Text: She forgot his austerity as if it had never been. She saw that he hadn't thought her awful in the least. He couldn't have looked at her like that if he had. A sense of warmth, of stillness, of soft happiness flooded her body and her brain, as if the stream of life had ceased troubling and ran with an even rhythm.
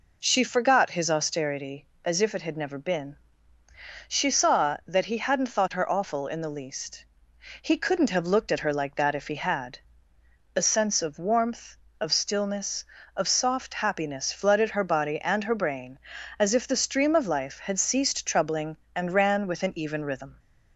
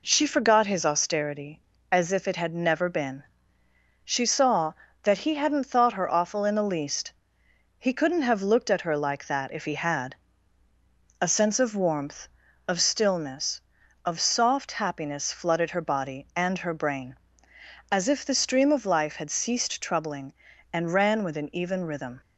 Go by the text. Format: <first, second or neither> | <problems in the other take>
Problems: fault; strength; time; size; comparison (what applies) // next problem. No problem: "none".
neither | none